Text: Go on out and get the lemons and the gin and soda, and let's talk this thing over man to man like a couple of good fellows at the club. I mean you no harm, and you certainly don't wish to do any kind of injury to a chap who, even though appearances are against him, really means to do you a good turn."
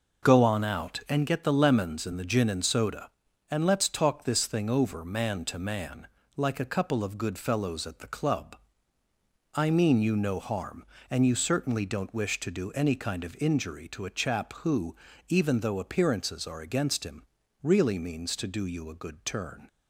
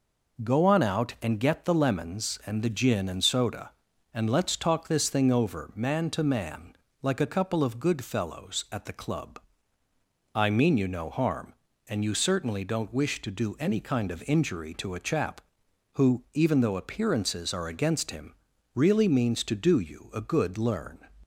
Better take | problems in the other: first | pauses between "man" and "like"; slight; at 6.7 s; 0.26 s long; slight in the first // says "learn" for "turn"; at 20.5 s

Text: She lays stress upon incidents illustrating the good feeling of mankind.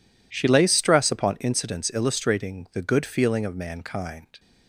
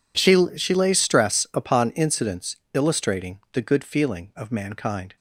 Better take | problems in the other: first | says "She" twice; at 0.5 s // pauses between "incidents" and "illustrating"; slight; at 2.5 s; 0.16 s long

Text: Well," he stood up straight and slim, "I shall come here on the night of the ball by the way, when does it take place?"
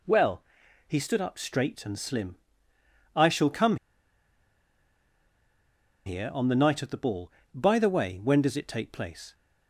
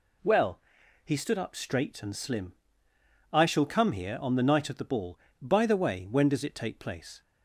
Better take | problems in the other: second | pauses between "come" and "here"; strong; at 3.7 s; 2.2 s long

